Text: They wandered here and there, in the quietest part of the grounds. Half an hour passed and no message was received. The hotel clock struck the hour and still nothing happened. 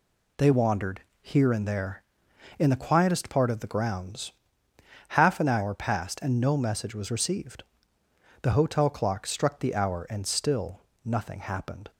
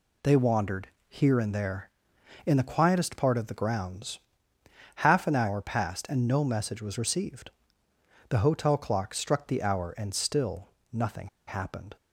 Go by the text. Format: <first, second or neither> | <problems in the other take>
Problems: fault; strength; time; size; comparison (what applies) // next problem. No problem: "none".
first | pauses between "wandered" and "here"; slight; at 0.8 s; 0.20 s long; slight in the first // pauses between "still" and "nothing"; slight; at 10.6 s; 0.24 s long; slight in the first // pauses between "nothing" and "happened"; slight; at 11.2 s; 0.19 s long